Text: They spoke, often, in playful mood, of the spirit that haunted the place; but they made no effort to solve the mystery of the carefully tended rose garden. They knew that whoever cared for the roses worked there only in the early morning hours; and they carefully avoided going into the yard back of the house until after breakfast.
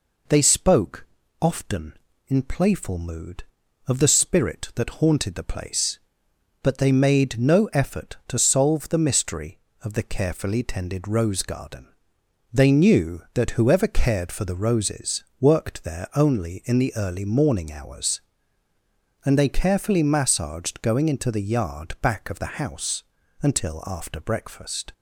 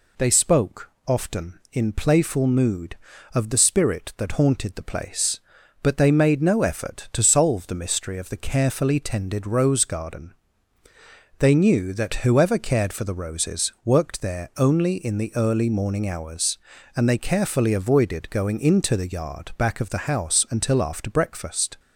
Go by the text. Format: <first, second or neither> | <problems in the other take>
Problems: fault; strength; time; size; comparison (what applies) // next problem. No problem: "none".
second | pauses between "roses" and "worked"; slight; at 15.2 s; 0.16 s long // says "massaged" for "avoided"; at 20.0 s // pauses between "house" and "until"; at 23.0 s; 0.40 s long